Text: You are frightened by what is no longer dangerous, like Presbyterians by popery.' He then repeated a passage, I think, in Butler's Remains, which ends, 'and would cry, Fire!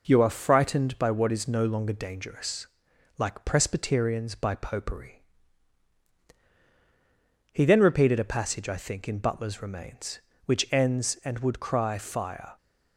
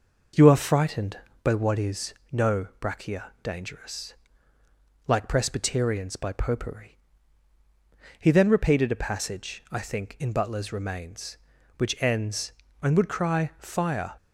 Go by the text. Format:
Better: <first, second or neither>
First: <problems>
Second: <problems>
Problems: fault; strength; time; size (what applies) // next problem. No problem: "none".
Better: first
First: none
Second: pauses between "is" and "no"; slight; at 2.1 s; 0.20 s long // says "brachia" for "longer"; at 2.8 s